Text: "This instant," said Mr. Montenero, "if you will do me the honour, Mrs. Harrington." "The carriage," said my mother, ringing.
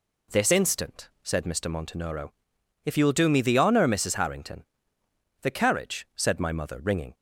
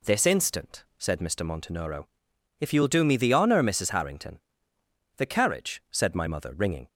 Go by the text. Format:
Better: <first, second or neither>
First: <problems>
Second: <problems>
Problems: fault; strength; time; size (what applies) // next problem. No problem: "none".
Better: neither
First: none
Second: none